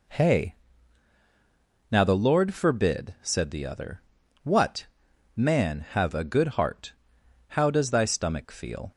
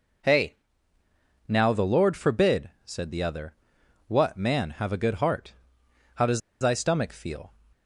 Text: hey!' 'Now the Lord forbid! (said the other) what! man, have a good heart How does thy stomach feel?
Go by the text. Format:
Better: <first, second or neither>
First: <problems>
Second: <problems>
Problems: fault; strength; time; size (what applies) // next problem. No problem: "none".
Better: first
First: pauses between "heart" and "How"; noticeable; at 6.9 s; 0.56 s long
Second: pauses between "heart" and "How"; noticeable; at 5.5 s; 0.64 s long // pauses between "does" and "thy"; slight; at 6.4 s; 0.20 s long